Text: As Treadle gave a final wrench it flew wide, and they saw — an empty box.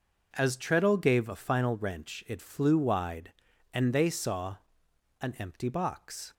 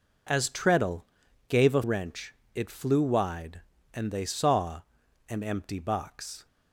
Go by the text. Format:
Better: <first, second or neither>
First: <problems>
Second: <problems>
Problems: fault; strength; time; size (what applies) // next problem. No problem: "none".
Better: first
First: none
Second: pauses between "Treadle" and "gave"; at 1.0 s; 0.42 s long // skips "final"; at 1.8 s // pauses between "wrench" and "it"; slight; at 2.3 s; 0.18 s long